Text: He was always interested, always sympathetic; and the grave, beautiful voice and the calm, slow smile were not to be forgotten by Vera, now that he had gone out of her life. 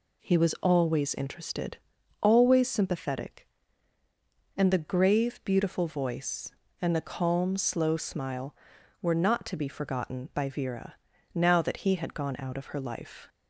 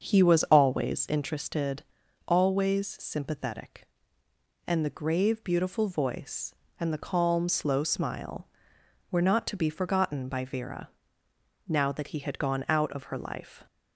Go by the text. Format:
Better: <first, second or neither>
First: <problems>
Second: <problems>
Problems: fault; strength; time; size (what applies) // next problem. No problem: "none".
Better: first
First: none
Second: starts louder than the rest; until 1.2 s; 7 dB